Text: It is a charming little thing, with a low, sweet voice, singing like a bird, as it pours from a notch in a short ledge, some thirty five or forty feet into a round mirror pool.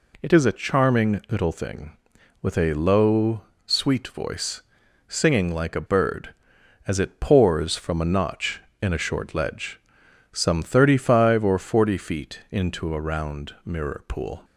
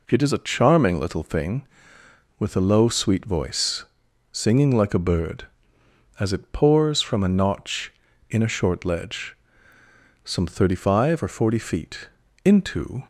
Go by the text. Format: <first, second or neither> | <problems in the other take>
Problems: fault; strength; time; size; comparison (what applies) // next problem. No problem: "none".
first | pauses between "feet" and "into"; slight; at 12.0 s; 0.34 s long // stops before "a round mirror pool"; at 13.0 s